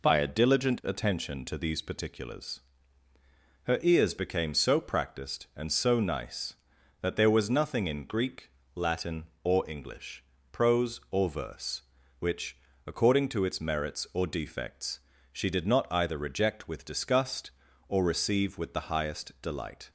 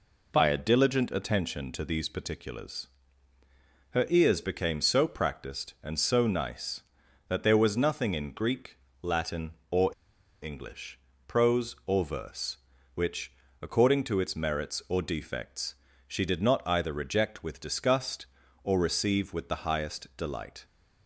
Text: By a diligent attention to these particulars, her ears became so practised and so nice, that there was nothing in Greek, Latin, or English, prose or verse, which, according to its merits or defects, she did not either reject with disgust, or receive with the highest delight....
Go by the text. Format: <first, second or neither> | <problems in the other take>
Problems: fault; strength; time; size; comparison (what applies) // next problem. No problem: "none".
first | pauses between "or" and "English"; noticeable; at 9.9 s; 0.54 s long